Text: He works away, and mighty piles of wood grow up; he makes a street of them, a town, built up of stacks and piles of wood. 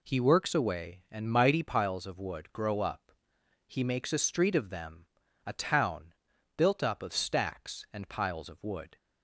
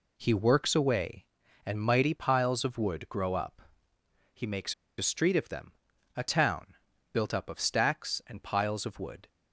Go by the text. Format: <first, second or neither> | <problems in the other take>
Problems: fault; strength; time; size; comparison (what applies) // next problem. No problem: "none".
first | pauses between "makes" and "a"; slight; at 4.7 s; 0.24 s long